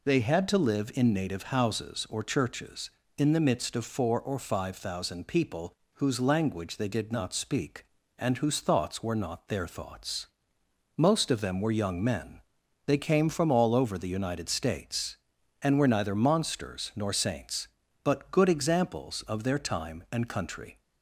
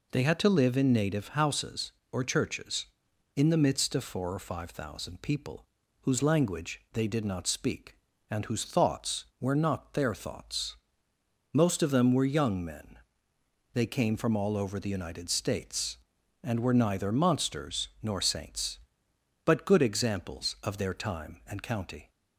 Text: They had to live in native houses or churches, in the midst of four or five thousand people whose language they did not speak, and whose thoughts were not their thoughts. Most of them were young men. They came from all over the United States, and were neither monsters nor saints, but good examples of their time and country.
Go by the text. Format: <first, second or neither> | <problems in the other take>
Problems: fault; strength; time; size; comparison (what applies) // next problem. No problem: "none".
first | pauses between "people" and "whose"; slight; at 5.6 s; 0.36 s long; slight in the first // says "county" for "country"; at 21.6 s